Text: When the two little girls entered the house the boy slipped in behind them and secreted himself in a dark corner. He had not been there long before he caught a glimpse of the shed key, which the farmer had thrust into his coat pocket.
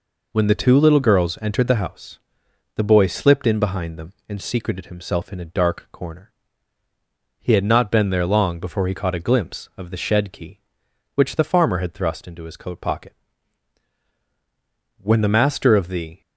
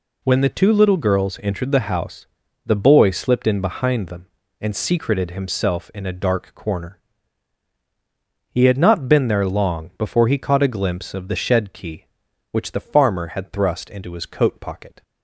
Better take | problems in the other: second | pauses between "house" and "the"; noticeable; at 2.1 s; 0.58 s long; also in the second // goes on to say "When the master of the"; noticeable; from 14.9 s on; 1.2 s long

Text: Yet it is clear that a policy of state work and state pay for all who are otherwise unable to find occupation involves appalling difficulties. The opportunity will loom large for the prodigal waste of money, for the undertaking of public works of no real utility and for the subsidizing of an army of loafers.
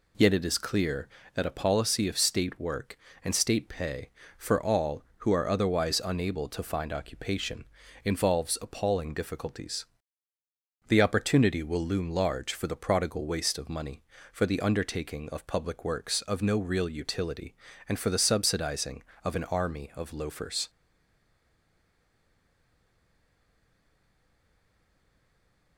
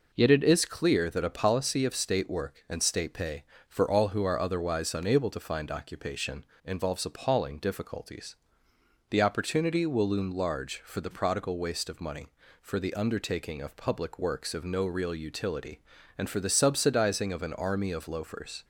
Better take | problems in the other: second | pauses between "occupation" and "involves"; at 7.6 s; 0.40 s long; slight in the second // stays silent after the last word; strong; from 20.6 s on; 5.1 s long

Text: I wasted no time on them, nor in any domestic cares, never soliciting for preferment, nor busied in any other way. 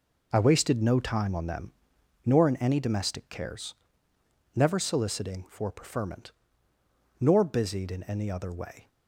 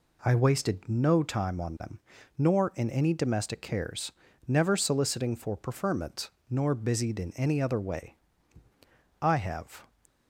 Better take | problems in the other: first | goes on to say "I have"; noticeable; from 9.2 s on; 0.72 s long

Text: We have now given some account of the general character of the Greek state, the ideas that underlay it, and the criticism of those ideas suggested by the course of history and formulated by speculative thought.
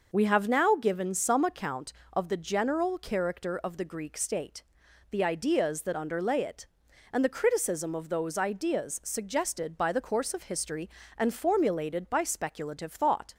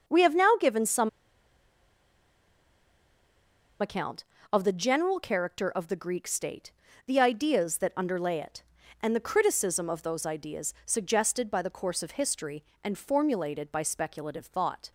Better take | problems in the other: first | starts louder than the rest; until 3.8 s; 6.5 dB // pauses between "some" and "account"; strong; at 1.0 s; 2.7 s long

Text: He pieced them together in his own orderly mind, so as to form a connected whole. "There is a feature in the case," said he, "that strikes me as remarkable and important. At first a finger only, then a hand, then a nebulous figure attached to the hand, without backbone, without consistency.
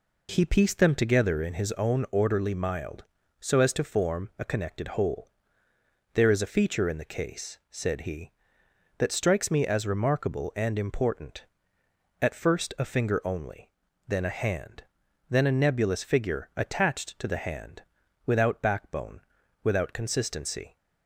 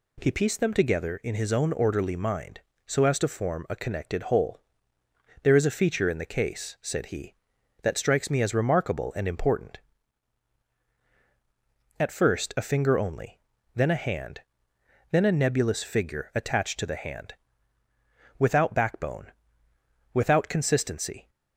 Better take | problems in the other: second | says "mild" for "mind"; at 2.5 s

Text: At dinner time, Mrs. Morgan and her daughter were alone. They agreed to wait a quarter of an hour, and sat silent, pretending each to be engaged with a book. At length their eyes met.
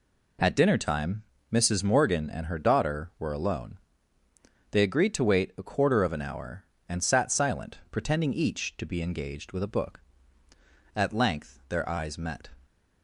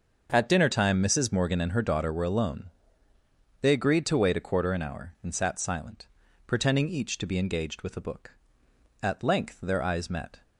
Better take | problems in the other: first | starts louder than the rest; until 1.3 s; 6.5 dB // skips "of"; at 4.7 s

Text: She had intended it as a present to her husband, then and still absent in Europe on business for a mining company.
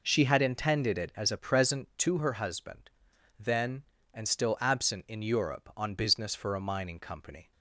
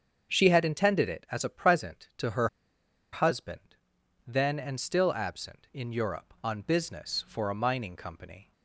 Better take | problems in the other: first | starts louder than the rest; strong; until 1.3 s; 7 dB // pauses between "her" and "husband"; noticeable; at 2.4 s; 0.66 s long

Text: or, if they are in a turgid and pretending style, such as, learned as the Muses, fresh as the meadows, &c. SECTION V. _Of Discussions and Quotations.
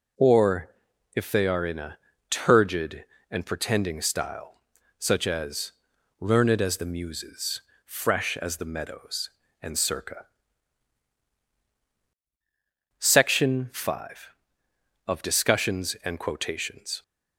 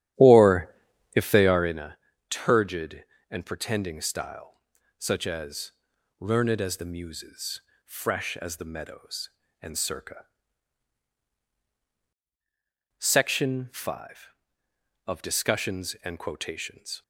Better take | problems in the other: first | starts louder than the rest; strong; until 1.9 s; 11.5 dB // pauses between "a" and "turgid"; slight; at 1.9 s; 0.32 s long; slight in the first

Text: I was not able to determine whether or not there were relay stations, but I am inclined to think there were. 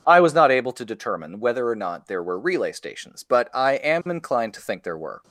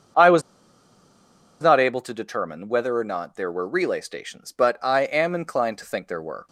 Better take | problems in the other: first | starts louder than the rest; until 2.3 s; 6.5 dB; also in the first // pauses between "was" and "not"; at 0.4 s; 1.2 s long

